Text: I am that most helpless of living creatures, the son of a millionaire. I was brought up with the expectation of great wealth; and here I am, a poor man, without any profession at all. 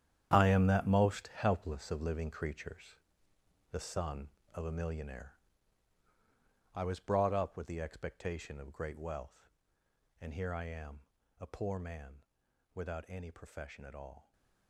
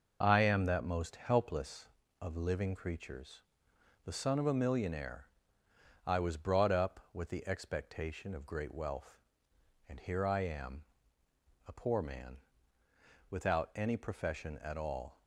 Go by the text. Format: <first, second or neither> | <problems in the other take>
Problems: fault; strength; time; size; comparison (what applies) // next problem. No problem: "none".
second | gets quieter; strong; throughout; 14 dB